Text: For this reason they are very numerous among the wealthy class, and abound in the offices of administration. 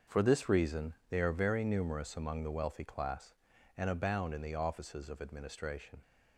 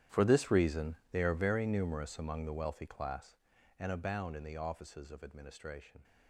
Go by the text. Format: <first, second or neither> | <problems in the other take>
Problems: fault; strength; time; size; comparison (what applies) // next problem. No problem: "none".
first | gets quieter; strong; throughout; 18.5 dB // starts louder than the rest; strong; until 1.2 s; 11 dB; also in the first // pauses between "reason" and "they"; slight; at 0.9 s; 0.16 s long; slight in the first